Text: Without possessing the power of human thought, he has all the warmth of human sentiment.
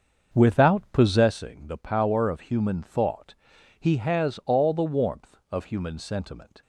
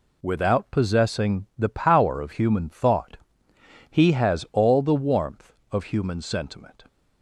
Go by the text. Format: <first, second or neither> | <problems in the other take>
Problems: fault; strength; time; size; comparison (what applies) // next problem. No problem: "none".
second | starts louder than the rest; until 1.3 s; 6.5 dB